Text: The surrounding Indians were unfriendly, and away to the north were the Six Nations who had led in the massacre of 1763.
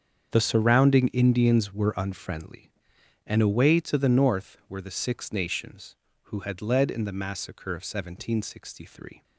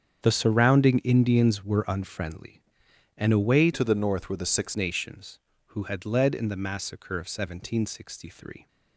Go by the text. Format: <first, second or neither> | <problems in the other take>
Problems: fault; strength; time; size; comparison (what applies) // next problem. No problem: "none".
first | starts louder than the rest; strong; until 1.2 s; 8 dB; strong in the first // changes voice from "to" to "Six"; from 3.7 to 4.7 s; 1.0 s long